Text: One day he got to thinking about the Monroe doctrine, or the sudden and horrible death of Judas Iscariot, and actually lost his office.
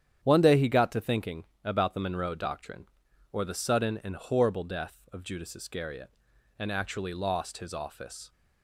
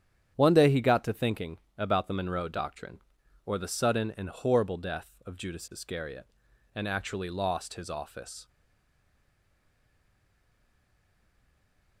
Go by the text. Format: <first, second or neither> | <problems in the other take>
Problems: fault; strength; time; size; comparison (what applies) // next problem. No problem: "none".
first | starts louder than the rest; strong; until 1.3 s; 9 dB; strong in the first // pauses between "thinking" and "about"; slight; at 1.5 s; 0.18 s long; slight in the first // stays silent after the last word; strong; from 8.4 s on; 3.6 s long